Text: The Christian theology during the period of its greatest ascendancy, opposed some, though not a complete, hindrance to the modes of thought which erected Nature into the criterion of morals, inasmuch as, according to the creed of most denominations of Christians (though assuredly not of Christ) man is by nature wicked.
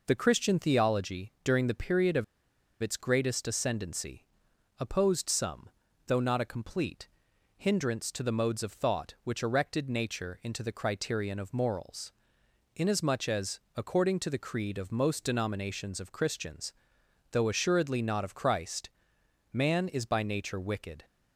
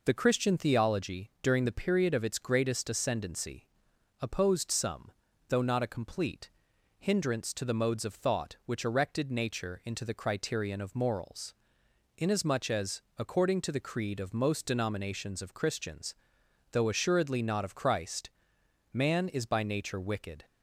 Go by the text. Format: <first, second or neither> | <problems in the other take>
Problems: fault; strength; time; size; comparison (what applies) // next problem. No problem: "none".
second | pauses between "of" and "its"; noticeable; at 2.2 s; 0.58 s long